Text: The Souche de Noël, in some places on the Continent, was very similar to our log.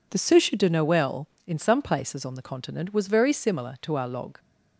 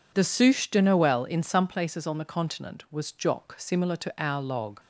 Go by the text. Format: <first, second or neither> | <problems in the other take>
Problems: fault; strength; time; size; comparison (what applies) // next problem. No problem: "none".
first | says "jock" for "very"; at 3.0 s